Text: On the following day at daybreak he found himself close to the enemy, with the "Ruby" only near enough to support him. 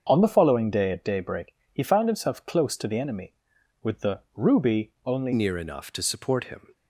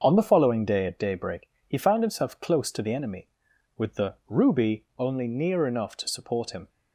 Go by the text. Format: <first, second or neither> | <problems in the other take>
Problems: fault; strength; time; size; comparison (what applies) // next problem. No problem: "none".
second | starts louder than the rest; until 1.0 s; 7 dB; also in the second // pauses between "daybreak" and "he"; slight; at 1.5 s; 0.20 s long; slight in the second // pauses between "the" and "Ruby"; slight; at 4.1 s; 0.18 s long; slight in the second // changes voice at "near"; from 5.3 s on; 1.4 s long